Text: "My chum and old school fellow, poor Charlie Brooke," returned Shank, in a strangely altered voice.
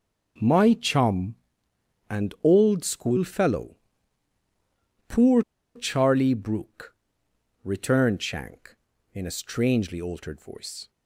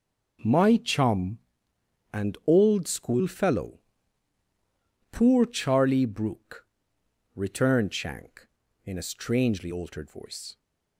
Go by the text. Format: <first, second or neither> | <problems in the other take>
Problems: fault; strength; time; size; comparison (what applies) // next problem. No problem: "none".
second | pauses between "poor" and "Charlie"; slight; at 5.4 s; 0.34 s long